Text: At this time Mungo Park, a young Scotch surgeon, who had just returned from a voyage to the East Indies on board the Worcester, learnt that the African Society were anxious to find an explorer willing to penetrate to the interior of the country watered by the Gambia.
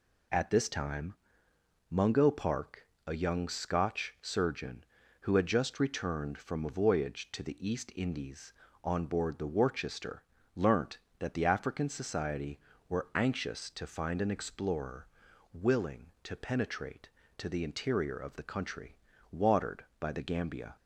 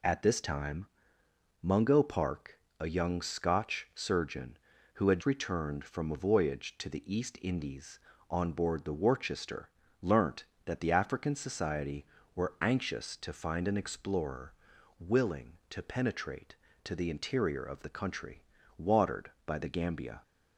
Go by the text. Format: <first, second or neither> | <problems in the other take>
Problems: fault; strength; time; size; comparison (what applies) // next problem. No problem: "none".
first | pauses between "time" and "Mungo"; noticeable; at 0.8 s; 0.74 s long; noticeable in the first // skips "just"; at 5.2 s // pauses between "explorer" and "willing"; noticeable; at 14.5 s; 0.48 s long; noticeable in the first // pauses between "country" and "watered"; slight; at 18.4 s; 0.36 s long; slight in the first